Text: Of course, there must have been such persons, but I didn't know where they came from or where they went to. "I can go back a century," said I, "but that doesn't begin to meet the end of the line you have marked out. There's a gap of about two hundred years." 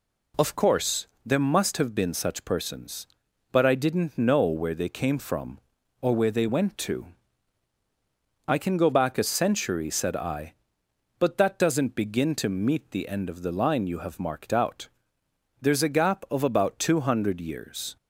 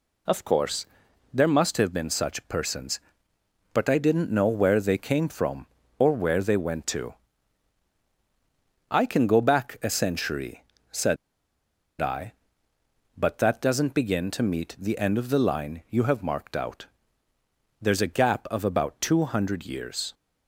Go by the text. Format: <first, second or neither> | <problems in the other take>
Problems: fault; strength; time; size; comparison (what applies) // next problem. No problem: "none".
first | pauses between "said" and "I"; noticeable; at 11.1 s; 0.85 s long